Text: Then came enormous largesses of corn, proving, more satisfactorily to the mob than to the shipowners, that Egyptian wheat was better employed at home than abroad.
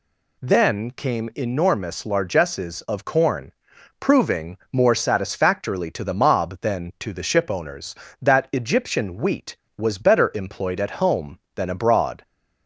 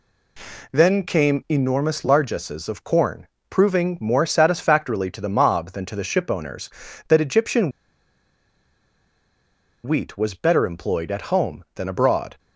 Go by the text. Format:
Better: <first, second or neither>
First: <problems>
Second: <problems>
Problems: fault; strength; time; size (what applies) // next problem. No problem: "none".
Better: first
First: none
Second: pauses between "Egyptian" and "wheat"; strong; at 7.7 s; 2.1 s long